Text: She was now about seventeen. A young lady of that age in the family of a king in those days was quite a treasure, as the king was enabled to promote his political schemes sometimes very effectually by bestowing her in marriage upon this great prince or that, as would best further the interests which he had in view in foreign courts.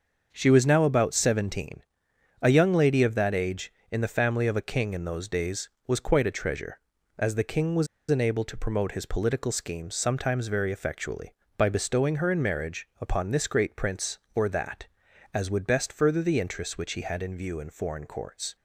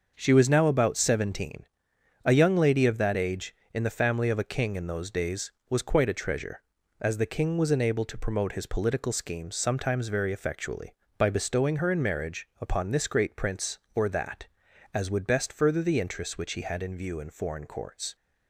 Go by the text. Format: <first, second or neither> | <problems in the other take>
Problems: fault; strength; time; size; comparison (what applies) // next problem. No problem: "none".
second | starts louder than the rest; until 1.3 s; 6.5 dB; also in the second // pauses between "was" and "enabled"; slight; at 7.8 s; 0.24 s long